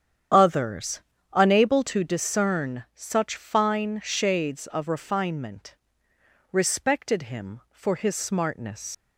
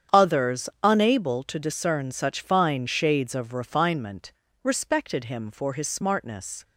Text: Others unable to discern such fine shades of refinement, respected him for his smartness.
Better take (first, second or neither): second